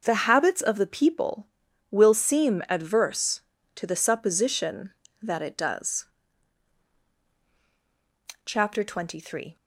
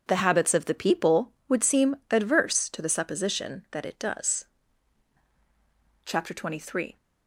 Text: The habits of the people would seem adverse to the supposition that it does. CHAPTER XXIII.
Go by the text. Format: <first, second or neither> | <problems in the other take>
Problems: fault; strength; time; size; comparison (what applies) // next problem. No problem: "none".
second | says "will" for "would"; at 1.8 s